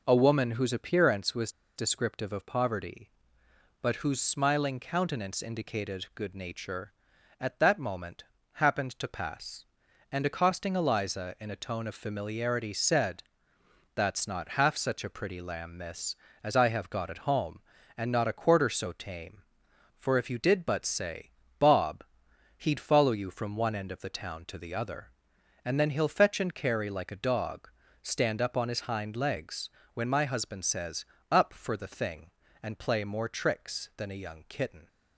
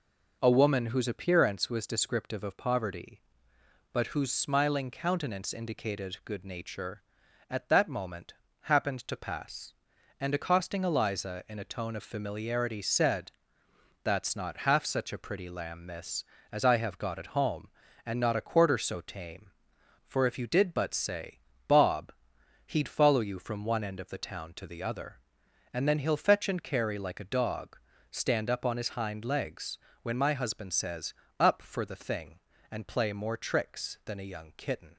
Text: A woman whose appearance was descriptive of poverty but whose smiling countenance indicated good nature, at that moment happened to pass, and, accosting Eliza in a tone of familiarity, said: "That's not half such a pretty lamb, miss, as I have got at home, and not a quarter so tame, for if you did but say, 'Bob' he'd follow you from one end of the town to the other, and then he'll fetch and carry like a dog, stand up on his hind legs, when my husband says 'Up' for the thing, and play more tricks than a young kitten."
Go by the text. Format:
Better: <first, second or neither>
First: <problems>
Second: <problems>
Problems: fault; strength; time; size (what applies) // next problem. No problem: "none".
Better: second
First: pauses between "was" and "descriptive"; slight; at 1.4 s; 0.26 s long // pauses between "moment" and "happened"; slight; at 8.2 s; 0.30 s long // pauses between "Bob" and "he'd"; noticeable; at 22.0 s; 0.54 s long // pauses between "says" and "Up"; slight; at 31.0 s; 0.24 s long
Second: pauses between "moment" and "happened"; slight; at 8.3 s; 0.28 s long // pauses between "Bob" and "he'd"; noticeable; at 22.1 s; 0.54 s long // pauses between "says" and "Up"; slight; at 31.1 s; 0.24 s long